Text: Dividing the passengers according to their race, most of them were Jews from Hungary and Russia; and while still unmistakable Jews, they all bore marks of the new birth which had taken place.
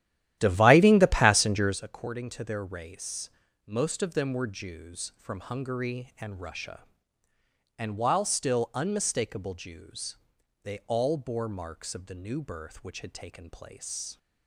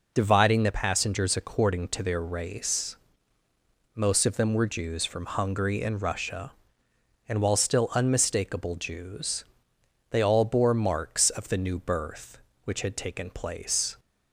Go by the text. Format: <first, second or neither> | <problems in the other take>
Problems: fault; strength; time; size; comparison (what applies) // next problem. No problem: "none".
second | starts louder than the rest; strong; until 1.9 s; 12.5 dB